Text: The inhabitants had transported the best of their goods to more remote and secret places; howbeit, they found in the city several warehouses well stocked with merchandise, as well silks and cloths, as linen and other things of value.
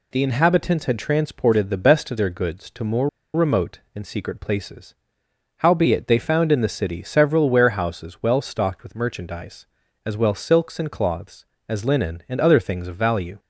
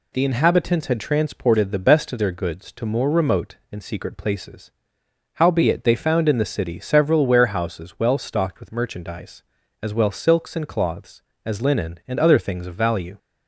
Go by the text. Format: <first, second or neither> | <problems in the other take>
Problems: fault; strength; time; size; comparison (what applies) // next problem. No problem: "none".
second | pauses between "more" and "remote"; slight; at 3.0 s; 0.26 s long